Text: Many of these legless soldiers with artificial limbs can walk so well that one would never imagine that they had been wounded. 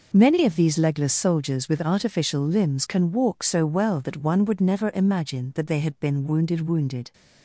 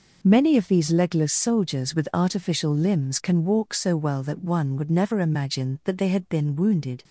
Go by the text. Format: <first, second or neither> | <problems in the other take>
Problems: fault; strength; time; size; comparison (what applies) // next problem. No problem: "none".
second | says "wounded" twice; at 6.6 s